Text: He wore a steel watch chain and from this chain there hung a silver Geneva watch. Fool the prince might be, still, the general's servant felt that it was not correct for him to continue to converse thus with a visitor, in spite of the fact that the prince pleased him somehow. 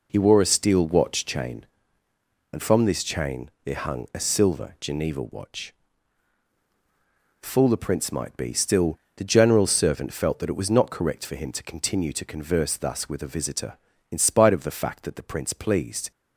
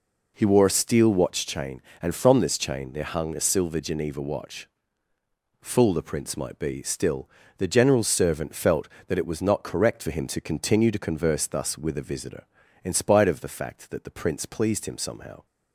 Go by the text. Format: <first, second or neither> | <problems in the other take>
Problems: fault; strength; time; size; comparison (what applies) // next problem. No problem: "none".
second | stops before "him somehow"; at 16.1 s